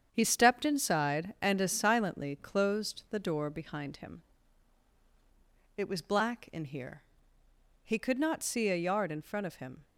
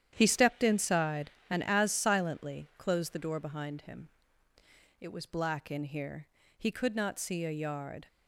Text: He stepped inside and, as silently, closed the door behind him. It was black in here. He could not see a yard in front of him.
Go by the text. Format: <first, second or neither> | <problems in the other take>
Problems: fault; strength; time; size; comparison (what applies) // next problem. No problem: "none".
first | starts louder than the rest; strong; until 1.1 s; 10 dB; strong in the first // stops before "in front of him"; at 8.0 s